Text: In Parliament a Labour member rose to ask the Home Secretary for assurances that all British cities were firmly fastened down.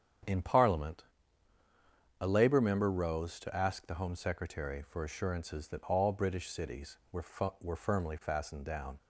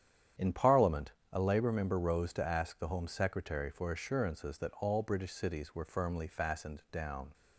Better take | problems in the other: second | starts louder than the rest; strong; until 2.4 s; 8 dB; strong in the second // pauses between "Parliament" and "a"; at 1.0 s; 1.1 s long; slight in the second // says "were" twice; at 7.5 s

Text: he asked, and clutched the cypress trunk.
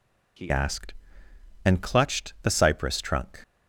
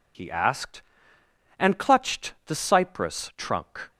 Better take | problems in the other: second | changes voice at "asked"; from 0.5 s on; 2.9 s long

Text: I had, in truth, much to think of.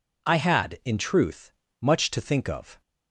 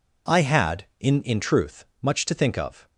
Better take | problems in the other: first | says "in" twice; at 1.2 s

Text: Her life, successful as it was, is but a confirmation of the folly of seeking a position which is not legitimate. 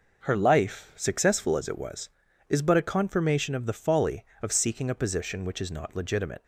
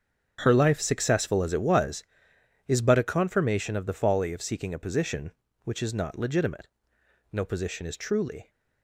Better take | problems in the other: first | starts louder than the rest; strong; until 1.4 s; 7.5 dB // goes on to say "No position is truly"; noticeable; from 7.3 s on; 1.1 s long

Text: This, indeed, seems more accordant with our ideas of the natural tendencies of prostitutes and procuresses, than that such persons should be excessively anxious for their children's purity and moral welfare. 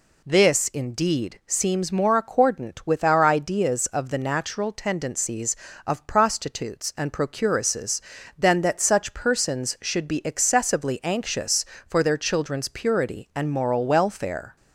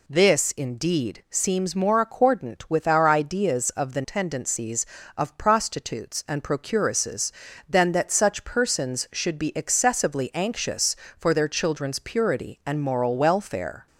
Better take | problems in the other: first | skips "natural"; at 4.0 s

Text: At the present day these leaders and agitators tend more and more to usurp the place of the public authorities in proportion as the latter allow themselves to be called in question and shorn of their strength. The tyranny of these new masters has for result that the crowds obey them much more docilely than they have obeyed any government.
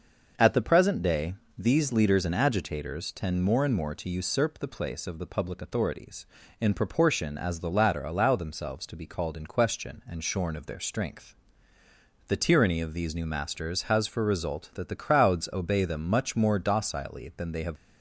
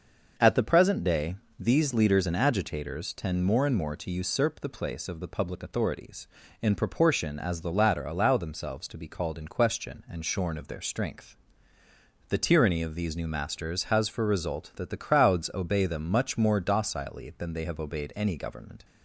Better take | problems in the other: second | starts louder than the rest; noticeable; until 1.6 s; 6 dB; noticeable in the second // pauses between "day" and "these"; slight; at 1.3 s; 0.22 s long; slight in the second // stops before "obeyed any government"; at 17.7 s

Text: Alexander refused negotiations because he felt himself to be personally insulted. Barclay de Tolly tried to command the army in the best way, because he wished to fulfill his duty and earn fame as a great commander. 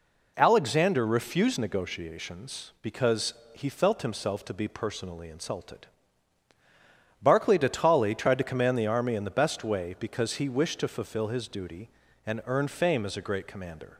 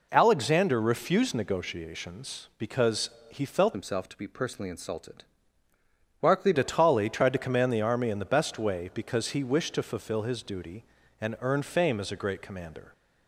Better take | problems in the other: first | pauses between "because" and "he"; slight; at 3.1 s; 0.18 s long; slight in the first // changes voice from "himself" to "Barclay"; from 3.7 to 6.5 s; 2.8 s long

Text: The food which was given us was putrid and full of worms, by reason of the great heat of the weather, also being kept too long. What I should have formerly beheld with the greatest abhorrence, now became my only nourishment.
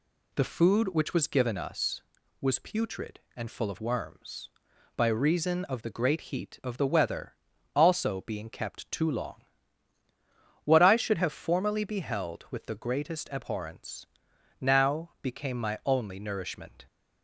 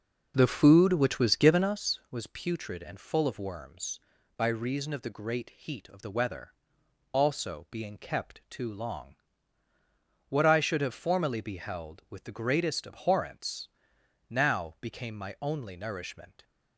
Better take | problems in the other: first | starts louder than the rest; noticeable; until 1.8 s; 5.5 dB

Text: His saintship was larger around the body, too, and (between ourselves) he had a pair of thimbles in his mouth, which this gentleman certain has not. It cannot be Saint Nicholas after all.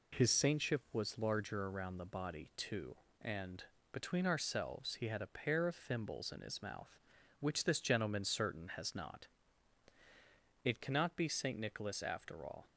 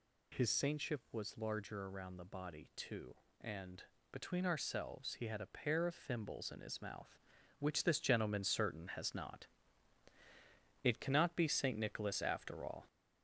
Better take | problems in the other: first | gets louder; slight; throughout; 3 dB

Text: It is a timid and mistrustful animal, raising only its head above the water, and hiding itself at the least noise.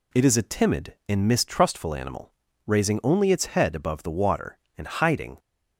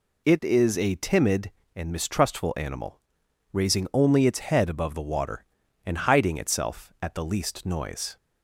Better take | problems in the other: second | stops before "itself at the least noise"; at 5.3 s

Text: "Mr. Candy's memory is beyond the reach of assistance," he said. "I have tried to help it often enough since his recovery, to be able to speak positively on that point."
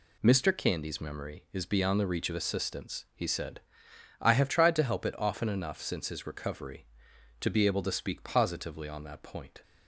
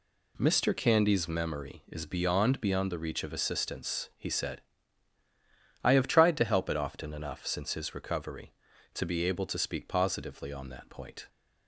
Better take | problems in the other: first | says "beyond" twice; at 2.6 s

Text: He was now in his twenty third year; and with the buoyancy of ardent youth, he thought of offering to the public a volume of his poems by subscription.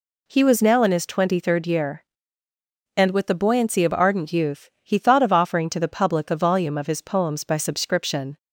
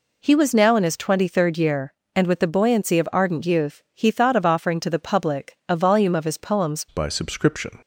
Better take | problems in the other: first | changes voice at "by"; from 6.8 s on; 0.9 s long

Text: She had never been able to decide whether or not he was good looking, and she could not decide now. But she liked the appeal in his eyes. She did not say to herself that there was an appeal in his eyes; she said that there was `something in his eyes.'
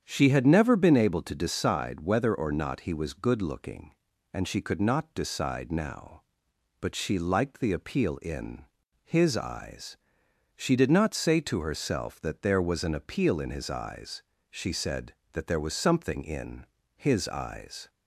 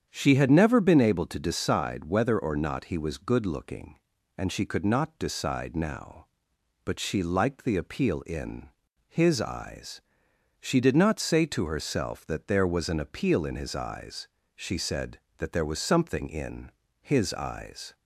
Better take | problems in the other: neither | starts louder than the rest; strong; the same in both // pauses between "in" and "his"; the same in both // pauses between "in" and "his"; slight; the same in both

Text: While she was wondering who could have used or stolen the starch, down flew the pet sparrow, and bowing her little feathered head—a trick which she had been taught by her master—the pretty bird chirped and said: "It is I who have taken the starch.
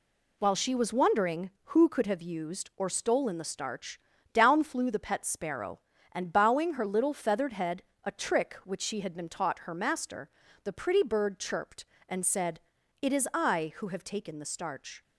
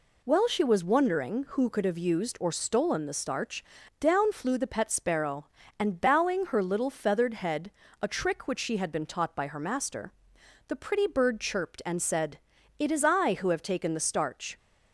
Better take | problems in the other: second | skips "by"; at 9.5 s

